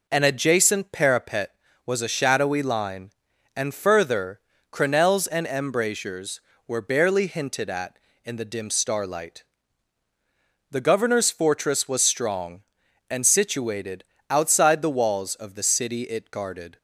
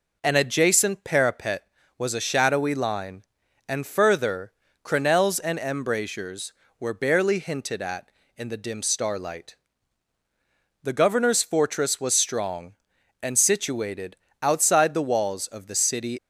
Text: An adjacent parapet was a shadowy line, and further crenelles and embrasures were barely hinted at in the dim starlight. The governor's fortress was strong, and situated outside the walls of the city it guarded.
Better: first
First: pauses between "further" and "crenelles"; slight; at 4.3 s; 0.32 s long // pauses between "situated" and "outside"; slight; at 14.0 s; 0.24 s long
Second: pauses between "further" and "crenelles"; slight; at 4.5 s; 0.32 s long // pauses between "situated" and "outside"; slight; at 14.1 s; 0.24 s long // stops before "it guarded"; at 16.1 s

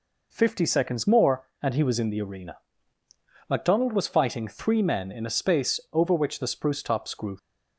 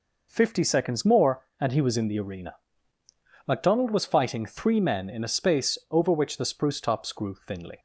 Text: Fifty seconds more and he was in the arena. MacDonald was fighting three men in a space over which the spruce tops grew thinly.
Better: second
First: stops before "thinly"; at 7.3 s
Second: none

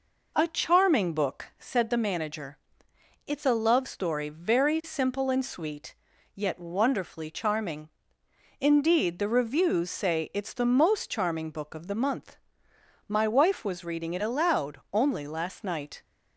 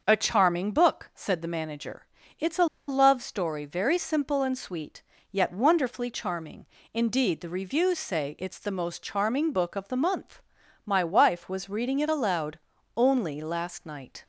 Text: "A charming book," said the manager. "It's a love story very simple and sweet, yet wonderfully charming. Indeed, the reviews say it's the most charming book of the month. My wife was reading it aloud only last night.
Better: first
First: none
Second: starts louder than the rest; until 1.0 s; 6.5 dB // pauses between "a" and "love"; slight; at 2.6 s; 0.22 s long // pauses between "aloud" and "only"; at 12.5 s; 0.38 s long

